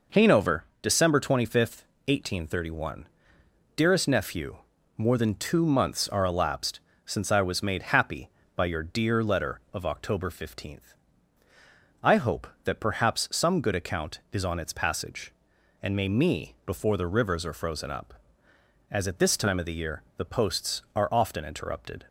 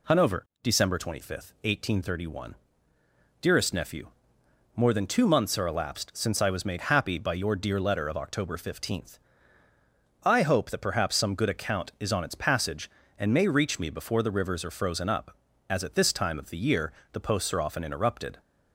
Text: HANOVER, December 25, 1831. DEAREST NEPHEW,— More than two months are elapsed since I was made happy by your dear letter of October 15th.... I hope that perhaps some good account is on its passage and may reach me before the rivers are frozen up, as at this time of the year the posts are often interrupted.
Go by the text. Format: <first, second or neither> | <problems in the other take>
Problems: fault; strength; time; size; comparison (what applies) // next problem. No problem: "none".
second | pauses between "elapsed" and "since"; slight; at 6.7 s; 0.26 s long // skips "reach"; at 16.0 s // pauses between "year" and "the"; slight; at 20.0 s; 0.16 s long; slight in the second